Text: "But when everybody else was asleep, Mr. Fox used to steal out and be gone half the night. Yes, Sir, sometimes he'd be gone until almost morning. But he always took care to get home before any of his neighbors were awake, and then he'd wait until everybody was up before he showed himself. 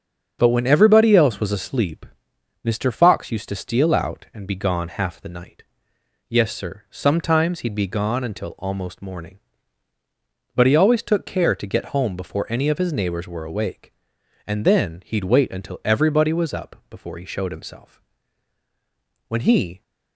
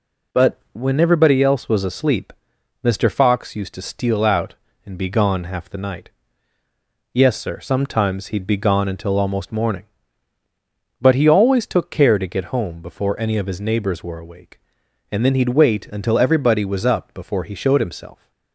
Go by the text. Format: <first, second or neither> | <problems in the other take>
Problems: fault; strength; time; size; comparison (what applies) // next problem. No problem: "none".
second | starts louder than the rest; until 1.4 s; 7 dB // goes on to say "When he"; from 19.2 s on; 0.54 s long